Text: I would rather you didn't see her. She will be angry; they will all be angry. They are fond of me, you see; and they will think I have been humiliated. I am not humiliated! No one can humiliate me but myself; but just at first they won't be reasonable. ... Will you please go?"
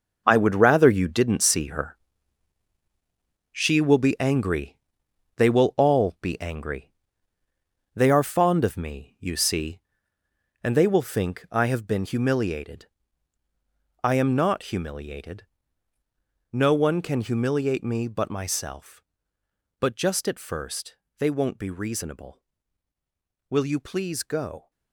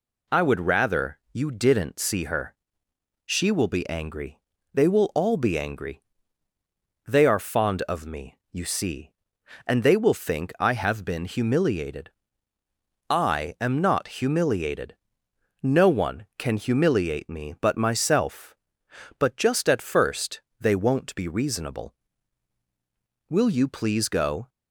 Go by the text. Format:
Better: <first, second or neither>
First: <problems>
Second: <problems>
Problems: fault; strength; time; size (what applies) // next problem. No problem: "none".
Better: second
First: gets quieter; strong; throughout; 10.5 dB // pauses between "first" and "they"; slight; at 20.9 s; 0.22 s long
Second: pauses between "first" and "they"; slight; at 20.4 s; 0.18 s long